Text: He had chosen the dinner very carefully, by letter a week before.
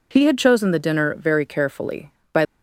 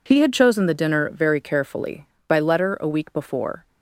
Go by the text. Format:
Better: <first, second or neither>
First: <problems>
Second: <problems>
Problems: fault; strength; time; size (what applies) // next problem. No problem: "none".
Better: second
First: stops before "letter a week before"; at 2.4 s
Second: none